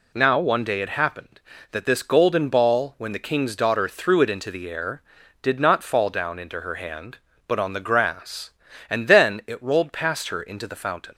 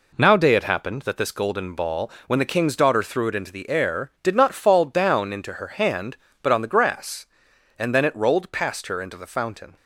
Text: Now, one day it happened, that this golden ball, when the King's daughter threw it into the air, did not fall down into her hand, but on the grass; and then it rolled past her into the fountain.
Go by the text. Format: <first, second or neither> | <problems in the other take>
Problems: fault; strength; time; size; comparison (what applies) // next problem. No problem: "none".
first | skips "one"; at 0.3 s